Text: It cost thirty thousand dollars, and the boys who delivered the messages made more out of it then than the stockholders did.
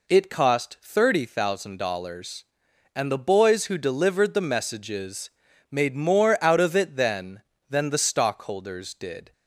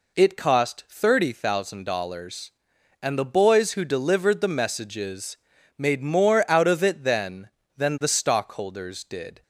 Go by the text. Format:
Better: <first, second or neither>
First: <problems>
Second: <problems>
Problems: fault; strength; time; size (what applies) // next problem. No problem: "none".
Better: neither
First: pauses between "messages" and "made"; at 5.3 s; 0.38 s long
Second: pauses between "messages" and "made"; at 5.3 s; 0.38 s long